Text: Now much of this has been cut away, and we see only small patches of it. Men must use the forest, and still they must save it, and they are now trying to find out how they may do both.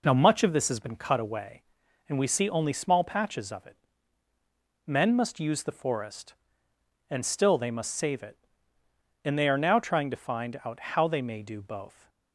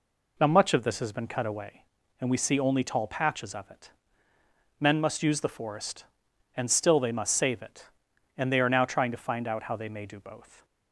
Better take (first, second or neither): first